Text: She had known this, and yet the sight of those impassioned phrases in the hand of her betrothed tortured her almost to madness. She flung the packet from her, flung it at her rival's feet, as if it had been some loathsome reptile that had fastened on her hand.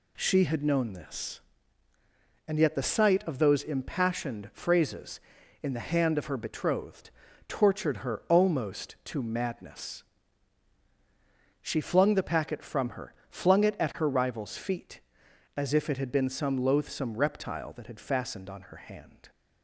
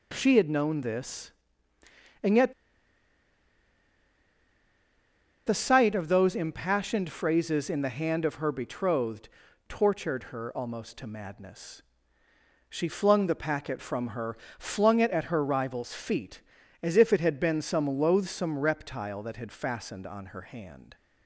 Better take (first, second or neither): first